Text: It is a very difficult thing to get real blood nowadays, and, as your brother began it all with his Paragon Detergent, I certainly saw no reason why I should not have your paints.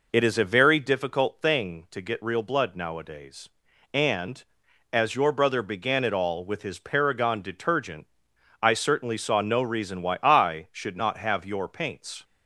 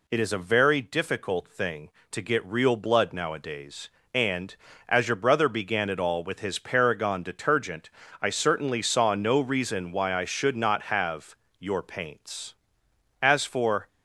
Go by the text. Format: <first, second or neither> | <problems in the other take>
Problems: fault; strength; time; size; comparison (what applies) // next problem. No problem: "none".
first | pauses between "have" and "your"; slight; at 11.3 s; 0.24 s long // goes on to say "As for"; noticeable; from 13.2 s on; 0.66 s long